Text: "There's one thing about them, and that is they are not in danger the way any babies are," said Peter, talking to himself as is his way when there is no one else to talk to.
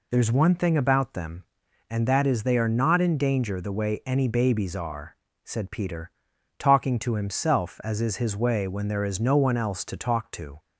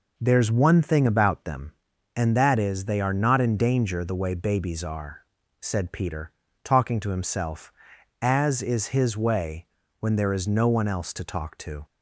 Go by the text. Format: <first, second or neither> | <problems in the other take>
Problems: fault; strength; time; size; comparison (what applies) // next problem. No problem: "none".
first | skips "any"; at 4.3 s // pauses between "way" and "when"; slight; at 9.6 s; 0.34 s long